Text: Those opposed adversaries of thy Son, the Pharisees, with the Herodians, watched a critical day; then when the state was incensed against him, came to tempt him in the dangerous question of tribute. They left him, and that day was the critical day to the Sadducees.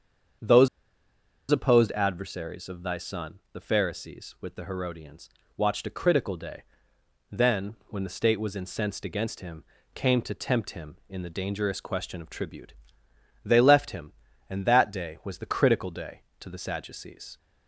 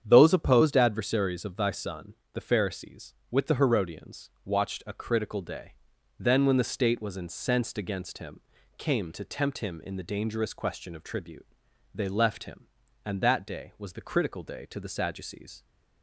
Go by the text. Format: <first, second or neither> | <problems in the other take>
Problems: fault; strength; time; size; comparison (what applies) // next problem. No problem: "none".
second | starts louder than the rest; strong; until 2.2 s; 7.5 dB; strong in the second // pauses between "Those" and "opposed"; noticeable; at 0.6 s; 0.83 s long